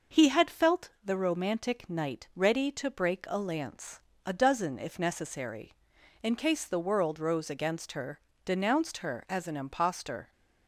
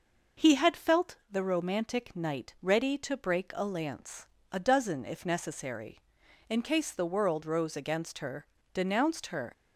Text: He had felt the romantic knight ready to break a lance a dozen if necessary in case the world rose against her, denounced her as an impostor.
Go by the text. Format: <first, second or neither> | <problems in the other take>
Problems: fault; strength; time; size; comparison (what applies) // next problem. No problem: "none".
first | pauses between "lance" and "a"; slight; at 4.2 s; 0.24 s long; slight in the first // stops before "as an impostor"; at 9.5 s